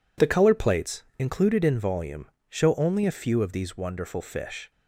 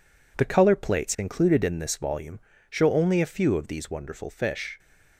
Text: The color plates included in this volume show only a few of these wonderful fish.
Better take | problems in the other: second | skips "this"; at 1.7 s // pauses between "volume" and "show"; slight; at 2.2 s; 0.24 s long; slight in the second

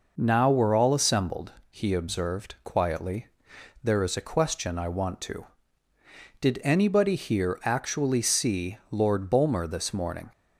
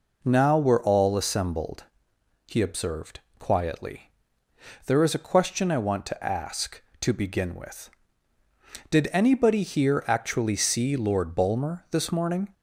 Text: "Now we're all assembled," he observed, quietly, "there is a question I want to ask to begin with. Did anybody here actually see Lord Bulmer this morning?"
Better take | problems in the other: second | skips "ask to begin with"; at 5.9 s

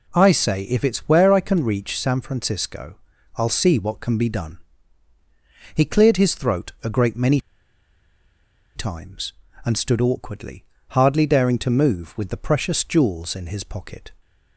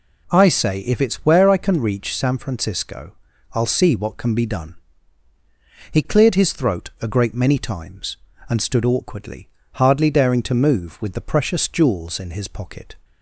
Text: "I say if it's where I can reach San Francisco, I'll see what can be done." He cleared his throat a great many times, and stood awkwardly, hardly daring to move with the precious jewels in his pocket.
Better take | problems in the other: second | pauses between "many" and "times"; strong; at 7.3 s; 1.3 s long

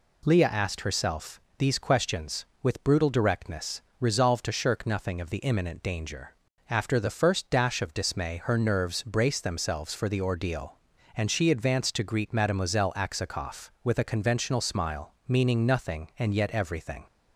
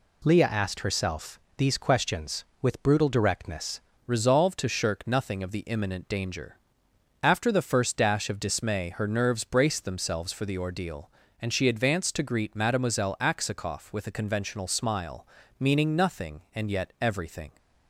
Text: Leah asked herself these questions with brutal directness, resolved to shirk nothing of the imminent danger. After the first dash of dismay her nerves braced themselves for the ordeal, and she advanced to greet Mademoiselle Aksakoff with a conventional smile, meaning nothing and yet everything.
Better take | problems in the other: first | pauses between "herself" and "these"; slight; at 1.3 s; 0.18 s long; slight in the first // changes voice at "resolved"; from 4.0 s on; 13.5 s long

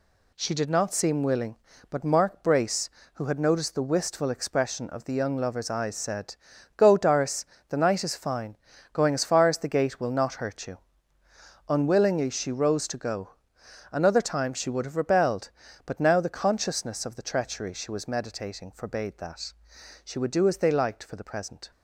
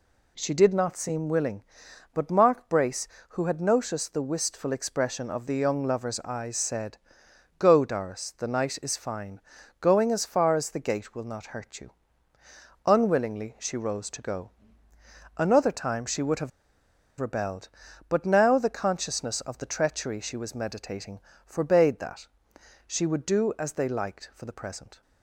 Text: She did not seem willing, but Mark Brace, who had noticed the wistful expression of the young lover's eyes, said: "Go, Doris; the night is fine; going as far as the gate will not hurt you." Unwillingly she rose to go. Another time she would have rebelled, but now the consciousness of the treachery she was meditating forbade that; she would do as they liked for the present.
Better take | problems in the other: first | pauses between "have" and "rebelled"; noticeable; at 16.5 s; 0.69 s long // pauses between "meditating" and "forbade"; slight; at 21.1 s; 0.26 s long

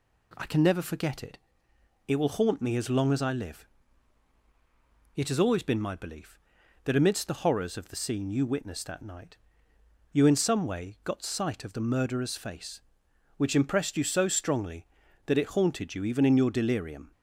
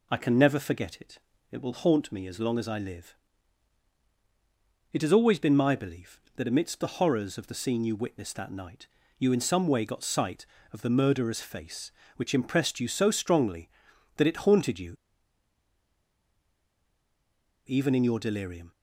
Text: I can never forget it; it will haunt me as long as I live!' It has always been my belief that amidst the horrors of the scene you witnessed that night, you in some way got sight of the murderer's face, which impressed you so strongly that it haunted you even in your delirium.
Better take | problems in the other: first | pauses between "you" and "even"; strong; at 14.9 s; 2.7 s long

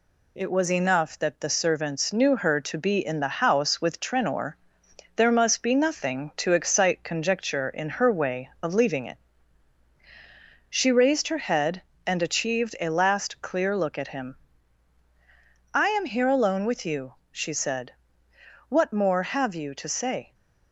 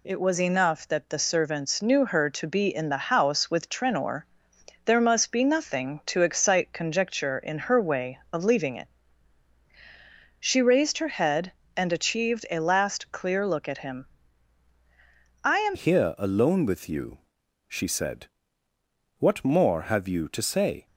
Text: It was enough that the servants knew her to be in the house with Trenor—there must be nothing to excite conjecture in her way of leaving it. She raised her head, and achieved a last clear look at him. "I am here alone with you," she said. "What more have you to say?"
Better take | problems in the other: first | changes voice at "here"; from 15.7 s on; 5.1 s long

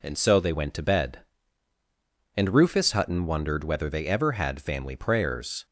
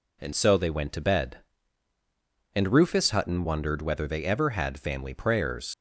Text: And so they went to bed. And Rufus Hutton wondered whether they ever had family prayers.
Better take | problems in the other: first | leaves "prayers" unfinished; at 5.7 s; 95 ms

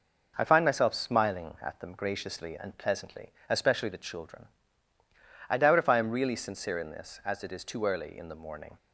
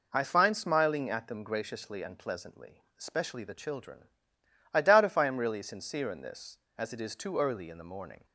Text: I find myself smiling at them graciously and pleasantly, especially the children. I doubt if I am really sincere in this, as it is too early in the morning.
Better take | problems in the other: first | skips "myself"; at 0.5 s

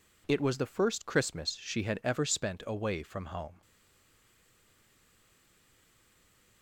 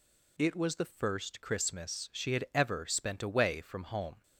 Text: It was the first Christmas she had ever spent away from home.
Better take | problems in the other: second | stays silent after the last word; strong; from 3.6 s on; 3.0 s long

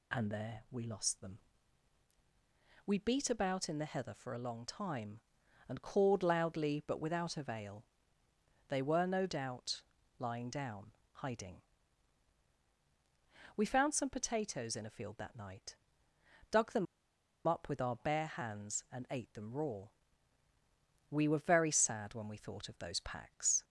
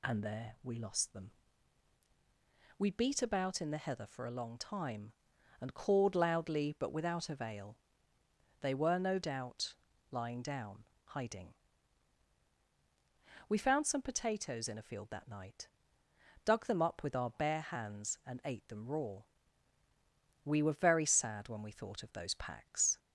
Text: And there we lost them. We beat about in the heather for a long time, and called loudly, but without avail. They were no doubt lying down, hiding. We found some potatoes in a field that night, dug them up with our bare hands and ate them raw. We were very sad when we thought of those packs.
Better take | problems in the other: second | pauses between "doubt" and "lying"; slight; at 9.8 s; 0.36 s long; slight in the second // pauses between "them" and "up"; noticeable; at 16.8 s; 0.62 s long

